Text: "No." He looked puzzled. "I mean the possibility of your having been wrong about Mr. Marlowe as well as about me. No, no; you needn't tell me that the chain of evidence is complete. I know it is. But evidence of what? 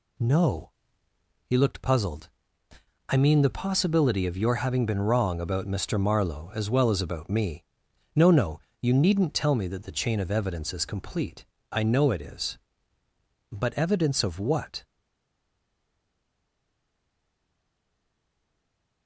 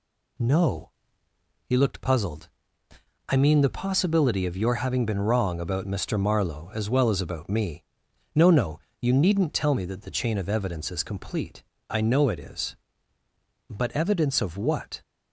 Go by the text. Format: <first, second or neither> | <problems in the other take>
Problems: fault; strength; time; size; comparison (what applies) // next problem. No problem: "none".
second | stays silent after the last word; strong; from 14.8 s on; 4.2 s long